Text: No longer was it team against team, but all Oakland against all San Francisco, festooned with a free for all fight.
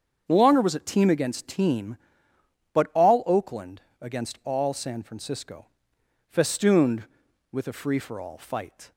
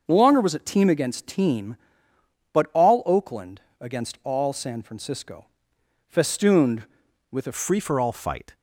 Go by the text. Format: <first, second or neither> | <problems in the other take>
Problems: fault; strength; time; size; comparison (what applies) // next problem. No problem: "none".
first | starts louder than the rest; noticeable; until 1.0 s; 6 dB; strong in the first // pauses between "Oakland" and "against"; slight; at 3.5 s; 0.20 s long; slight in the first // changes voice at "free"; from 7.5 s on; 1.0 s long